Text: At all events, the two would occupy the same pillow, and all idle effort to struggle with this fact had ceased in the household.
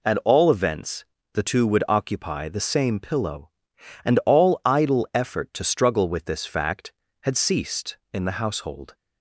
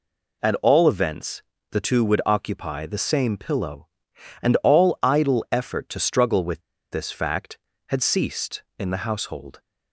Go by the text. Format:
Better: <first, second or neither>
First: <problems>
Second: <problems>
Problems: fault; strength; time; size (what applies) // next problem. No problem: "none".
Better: first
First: none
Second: pauses between "with" and "this"; slight; at 6.6 s; 0.30 s long